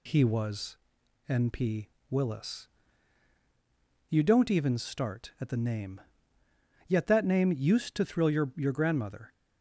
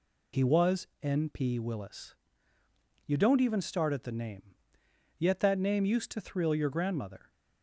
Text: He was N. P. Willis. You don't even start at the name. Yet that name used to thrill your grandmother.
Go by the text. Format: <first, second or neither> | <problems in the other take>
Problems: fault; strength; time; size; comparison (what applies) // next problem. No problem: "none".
second | pauses between "was" and "N"; noticeable; at 0.7 s; 0.52 s long // pauses between "P" and "Willis"; slight; at 1.8 s; 0.22 s long // says "your" twice; at 8.5 s